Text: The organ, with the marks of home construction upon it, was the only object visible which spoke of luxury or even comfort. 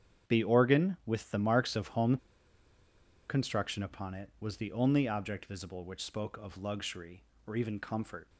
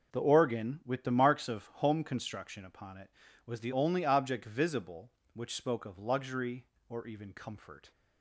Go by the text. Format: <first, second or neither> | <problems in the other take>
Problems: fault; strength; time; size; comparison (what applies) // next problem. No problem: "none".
second | starts louder than the rest; strong; until 1.3 s; 8.5 dB // pauses between "home" and "construction"; at 2.1 s; 1.1 s long